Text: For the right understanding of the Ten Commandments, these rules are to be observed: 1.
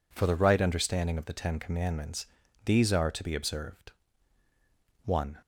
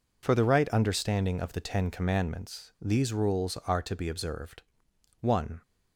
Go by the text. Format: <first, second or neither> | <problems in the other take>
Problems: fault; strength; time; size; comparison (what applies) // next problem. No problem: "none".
second | skips "rules"; at 2.9 s